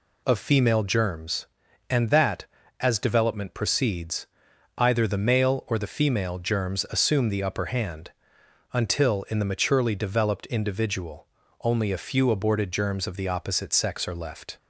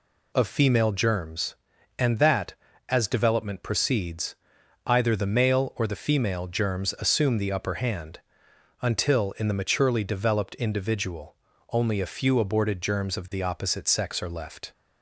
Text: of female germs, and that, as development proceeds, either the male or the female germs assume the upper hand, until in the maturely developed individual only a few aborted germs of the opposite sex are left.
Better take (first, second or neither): neither